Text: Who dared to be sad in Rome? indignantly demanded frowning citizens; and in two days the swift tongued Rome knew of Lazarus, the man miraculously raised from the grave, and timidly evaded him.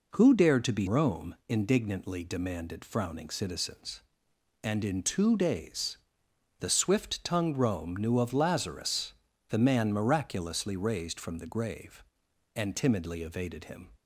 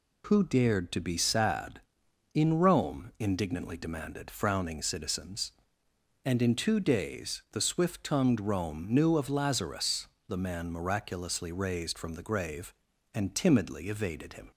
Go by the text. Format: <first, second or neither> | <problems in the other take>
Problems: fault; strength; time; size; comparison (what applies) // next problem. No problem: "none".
second | skips "sad in"; at 0.8 s // pauses between "days" and "the"; noticeable; at 5.9 s; 0.62 s long